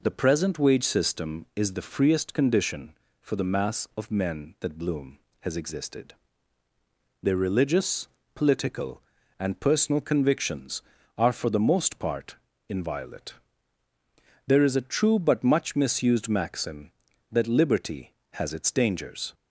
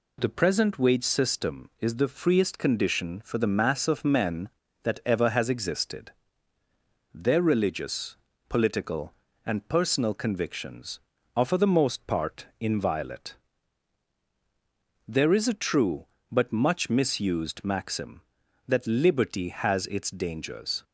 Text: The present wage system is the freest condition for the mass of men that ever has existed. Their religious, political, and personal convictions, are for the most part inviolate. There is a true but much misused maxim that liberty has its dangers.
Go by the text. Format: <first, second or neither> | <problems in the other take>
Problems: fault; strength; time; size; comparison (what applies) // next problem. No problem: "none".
second | says "bloom" for "ever"; at 4.7 s // pauses between "part" and "inviolate"; slight; at 12.3 s; 0.32 s long